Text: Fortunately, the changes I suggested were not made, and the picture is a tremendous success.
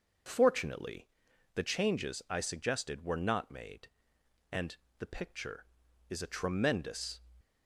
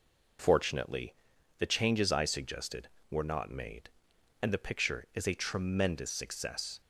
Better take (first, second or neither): second